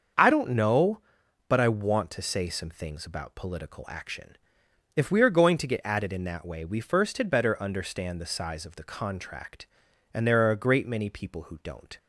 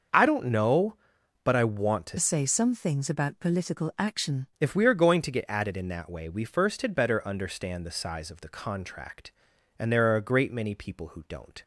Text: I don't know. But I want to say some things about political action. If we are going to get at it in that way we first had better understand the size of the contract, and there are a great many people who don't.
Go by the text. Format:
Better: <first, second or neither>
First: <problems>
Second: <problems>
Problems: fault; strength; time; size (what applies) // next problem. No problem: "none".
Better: first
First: starts louder than the rest; until 1.6 s; 6.5 dB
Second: starts louder than the rest; until 1.6 s; 6.5 dB // changes voice from "say" to "action"; from 2.1 to 4.4 s; 2.3 s long